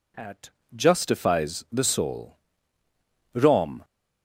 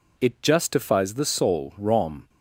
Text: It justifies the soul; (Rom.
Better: second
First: says "At" for "It"; at 0.1 s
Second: none

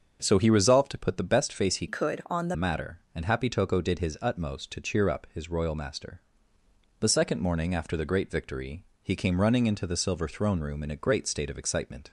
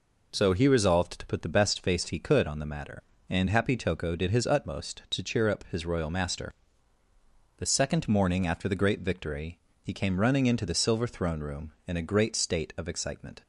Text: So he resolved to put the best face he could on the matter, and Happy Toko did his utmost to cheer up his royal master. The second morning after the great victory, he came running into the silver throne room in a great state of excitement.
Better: second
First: starts louder than the rest; until 1.2 s; 6.5 dB // changes voice from "could" to "the"; from 1.8 to 2.5 s; 0.7 s long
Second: none

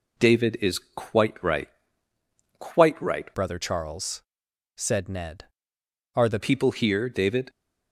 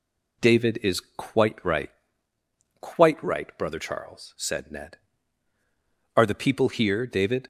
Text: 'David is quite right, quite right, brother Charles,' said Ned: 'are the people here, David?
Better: second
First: changes voice from "brother" to "the"; from 3.3 to 6.3 s; 3.0 s long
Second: none

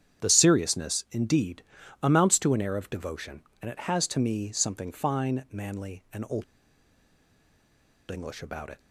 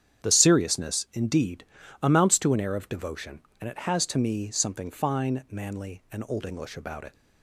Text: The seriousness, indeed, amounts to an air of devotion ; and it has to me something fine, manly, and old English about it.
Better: second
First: starts louder than the rest; strong; until 1.3 s; 8.5 dB // pauses between "old" and "English"; strong; at 6.4 s; 1.6 s long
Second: starts louder than the rest; strong; until 1.3 s; 8.5 dB

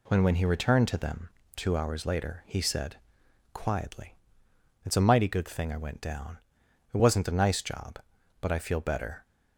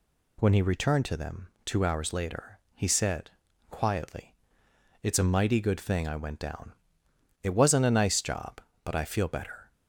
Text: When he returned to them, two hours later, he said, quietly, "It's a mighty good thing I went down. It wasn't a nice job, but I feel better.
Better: second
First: says "When" twice; at 0.2 s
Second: none

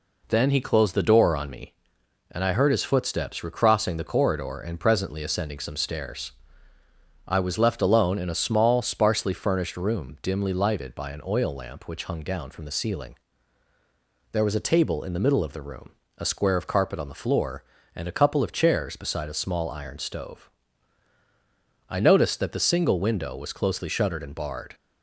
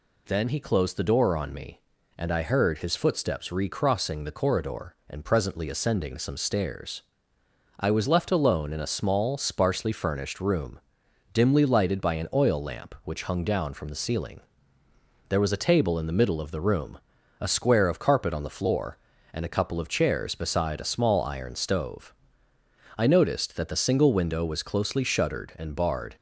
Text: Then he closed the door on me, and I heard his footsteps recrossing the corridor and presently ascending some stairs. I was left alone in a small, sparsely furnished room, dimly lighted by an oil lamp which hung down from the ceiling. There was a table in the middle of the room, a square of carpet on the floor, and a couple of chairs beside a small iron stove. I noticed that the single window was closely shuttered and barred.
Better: neither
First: none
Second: none

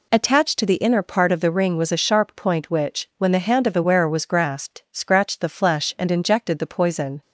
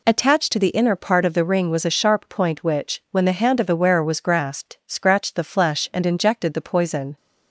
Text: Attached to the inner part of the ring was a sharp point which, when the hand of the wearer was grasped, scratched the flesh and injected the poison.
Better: neither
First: none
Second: none

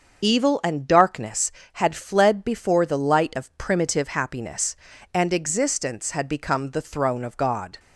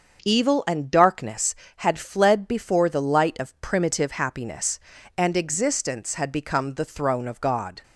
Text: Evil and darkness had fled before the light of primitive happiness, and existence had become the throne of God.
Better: second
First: loses the start of "Evil"; at 0.2 s; 60 ms // starts louder than the rest; until 1.2 s; 6.5 dB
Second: starts louder than the rest; until 1.2 s; 6.5 dB

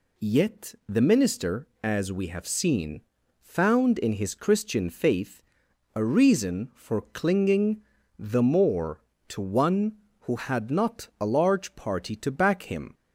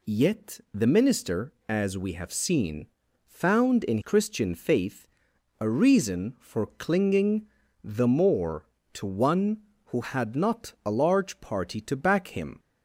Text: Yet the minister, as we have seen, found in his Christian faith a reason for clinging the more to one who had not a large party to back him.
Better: first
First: pauses between "faith" and "a"; noticeable; at 5.4 s; 0.52 s long // pauses between "clinging" and "the"; slight; at 7.8 s; 0.36 s long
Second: skips "his"; at 4.0 s // pauses between "faith" and "a"; noticeable; at 5.0 s; 0.52 s long // pauses between "clinging" and "the"; slight; at 7.4 s; 0.36 s long

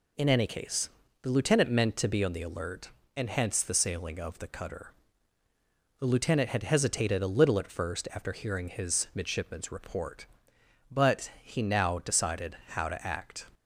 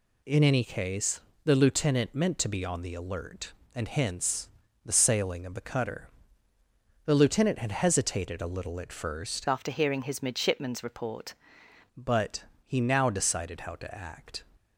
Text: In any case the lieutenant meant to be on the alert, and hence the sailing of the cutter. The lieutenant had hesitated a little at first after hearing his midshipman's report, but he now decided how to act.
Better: first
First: pauses between "case" and "the"; slight; at 0.8 s; 0.34 s long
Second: pauses between "case" and "the"; slight; at 1.2 s; 0.24 s long // pauses between "hence" and "the"; slight; at 4.4 s; 0.36 s long // changes voice from "after" to "report"; from 9.4 to 11.3 s; 1.9 s long // pauses between "but" and "he"; slight; at 12.4 s; 0.20 s long

